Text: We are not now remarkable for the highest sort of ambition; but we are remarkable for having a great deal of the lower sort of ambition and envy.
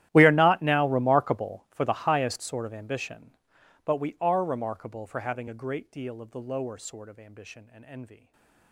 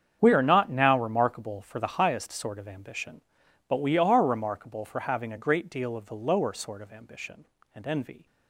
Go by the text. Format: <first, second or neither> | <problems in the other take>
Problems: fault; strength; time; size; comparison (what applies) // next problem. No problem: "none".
second | gets quieter; strong; throughout; 22 dB // starts louder than the rest; strong; until 1.1 s; 13.5 dB; strong in the second // stays silent after the last word; slight; from 8.1 s on; 0.6 s long